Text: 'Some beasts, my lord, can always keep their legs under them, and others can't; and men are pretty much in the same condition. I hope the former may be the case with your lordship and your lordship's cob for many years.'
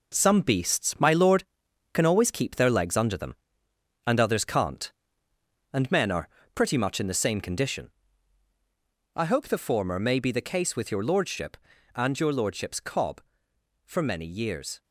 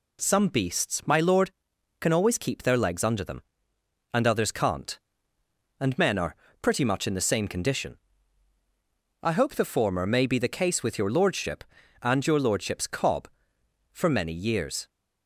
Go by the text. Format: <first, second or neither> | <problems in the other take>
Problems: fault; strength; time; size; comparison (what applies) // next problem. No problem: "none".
second | gets quieter; strong; throughout; 7.5 dB // pauses between "are" and "pretty"; slight; at 6.2 s; 0.24 s long; slight in the second